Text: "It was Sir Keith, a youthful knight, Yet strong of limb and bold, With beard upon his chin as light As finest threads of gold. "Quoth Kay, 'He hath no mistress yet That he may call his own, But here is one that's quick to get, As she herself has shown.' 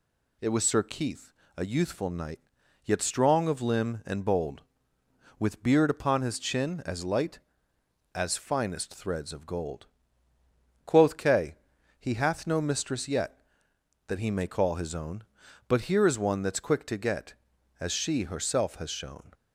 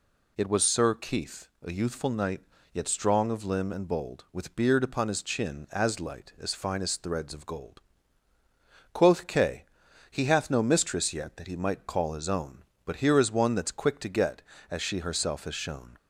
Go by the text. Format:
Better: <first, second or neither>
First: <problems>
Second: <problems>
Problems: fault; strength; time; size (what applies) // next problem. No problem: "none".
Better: first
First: none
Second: says "might" for "may"; at 11.5 s